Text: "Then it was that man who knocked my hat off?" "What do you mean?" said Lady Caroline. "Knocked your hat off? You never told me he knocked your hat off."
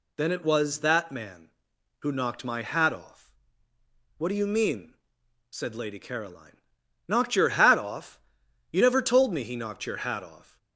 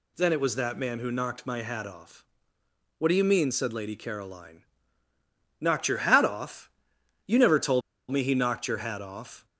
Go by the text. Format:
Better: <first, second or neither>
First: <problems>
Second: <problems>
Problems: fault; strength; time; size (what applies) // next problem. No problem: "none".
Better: first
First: none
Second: pauses between "told" and "me"; slight; at 7.8 s; 0.30 s long